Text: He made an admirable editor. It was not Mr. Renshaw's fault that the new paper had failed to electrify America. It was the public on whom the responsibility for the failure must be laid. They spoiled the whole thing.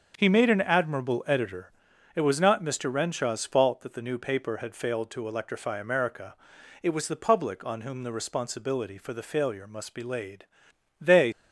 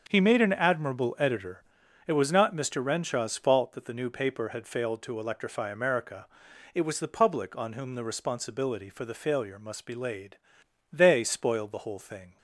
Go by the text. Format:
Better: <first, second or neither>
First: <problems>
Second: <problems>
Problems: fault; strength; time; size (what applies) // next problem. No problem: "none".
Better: second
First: starts louder than the rest; until 1.1 s; 7 dB // stops before "spoiled the whole thing"; at 11.3 s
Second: starts louder than the rest; until 1.0 s; 7 dB